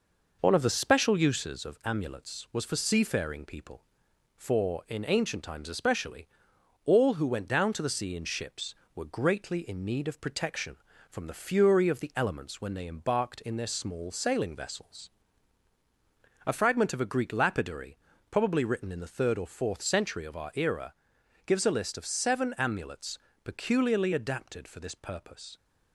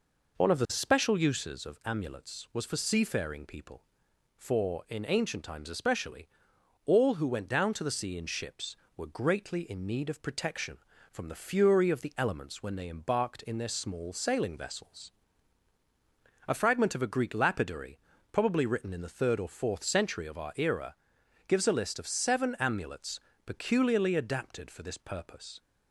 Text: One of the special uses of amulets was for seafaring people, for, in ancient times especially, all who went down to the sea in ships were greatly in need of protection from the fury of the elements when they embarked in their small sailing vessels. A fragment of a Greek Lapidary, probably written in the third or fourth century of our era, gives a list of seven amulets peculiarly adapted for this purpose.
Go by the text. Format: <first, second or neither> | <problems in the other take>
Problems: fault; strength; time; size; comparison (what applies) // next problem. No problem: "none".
second | gets quieter; slight; throughout; 3 dB // pauses between "amulets" and "peculiarly"; slight; at 23.1 s; 0.26 s long; slight in the second